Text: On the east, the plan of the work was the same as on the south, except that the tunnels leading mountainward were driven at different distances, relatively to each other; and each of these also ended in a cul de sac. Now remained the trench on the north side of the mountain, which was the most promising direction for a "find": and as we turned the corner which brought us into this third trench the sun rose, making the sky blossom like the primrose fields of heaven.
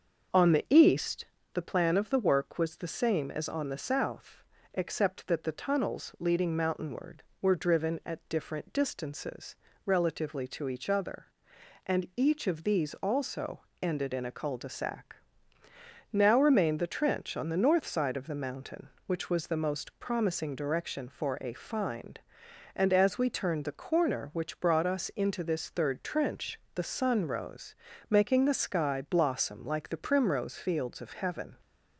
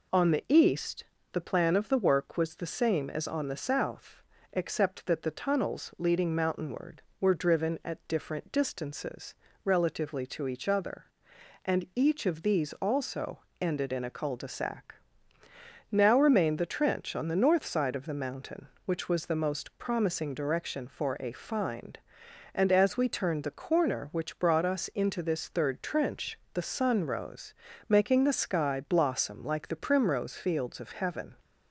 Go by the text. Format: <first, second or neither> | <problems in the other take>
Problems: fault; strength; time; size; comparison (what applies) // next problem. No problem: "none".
second | starts louder than the rest; until 1.4 s; 6.5 dB // pauses between "also" and "ended"; slight; at 13.6 s; 0.22 s long; slight in the second // pauses between "trench" and "the"; slight; at 26.5 s; 0.16 s long; slight in the second